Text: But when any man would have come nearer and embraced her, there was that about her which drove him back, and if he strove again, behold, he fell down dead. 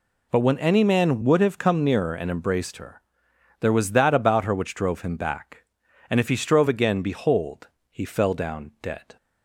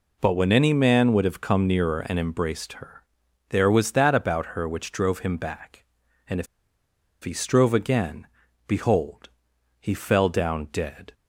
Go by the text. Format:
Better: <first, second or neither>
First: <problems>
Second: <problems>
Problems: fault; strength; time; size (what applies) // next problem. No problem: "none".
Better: first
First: none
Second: pauses between "if" and "he"; noticeable; at 6.4 s; 0.76 s long